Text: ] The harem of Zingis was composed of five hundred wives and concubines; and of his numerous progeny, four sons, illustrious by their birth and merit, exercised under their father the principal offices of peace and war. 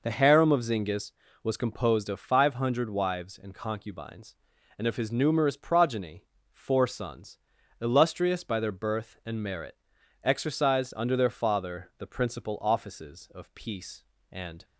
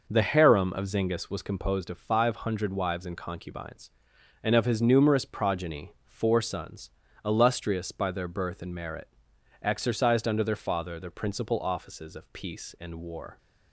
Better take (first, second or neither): second